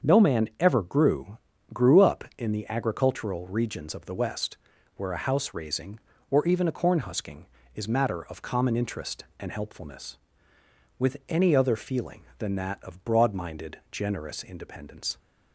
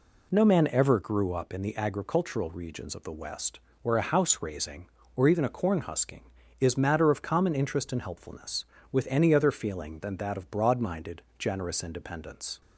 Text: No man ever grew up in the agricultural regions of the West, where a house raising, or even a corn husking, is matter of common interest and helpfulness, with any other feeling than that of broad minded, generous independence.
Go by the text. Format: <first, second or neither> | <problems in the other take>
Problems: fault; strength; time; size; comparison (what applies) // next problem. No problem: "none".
second | starts louder than the rest; until 1.1 s; 6.5 dB // says "grew" twice; at 1.7 s